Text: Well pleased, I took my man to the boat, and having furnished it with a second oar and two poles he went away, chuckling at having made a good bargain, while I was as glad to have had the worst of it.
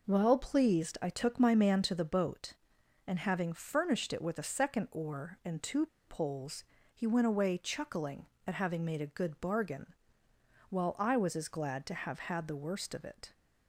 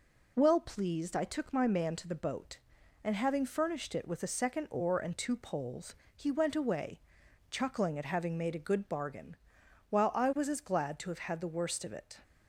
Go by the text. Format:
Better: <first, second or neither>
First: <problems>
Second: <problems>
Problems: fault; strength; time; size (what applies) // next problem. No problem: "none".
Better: second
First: pauses between "two" and "poles"; slight; at 5.8 s; 0.21 s long // pauses between "poles" and "he"; slight; at 6.6 s; 0.32 s long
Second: pauses between "poles" and "he"; slight; at 5.9 s; 0.20 s long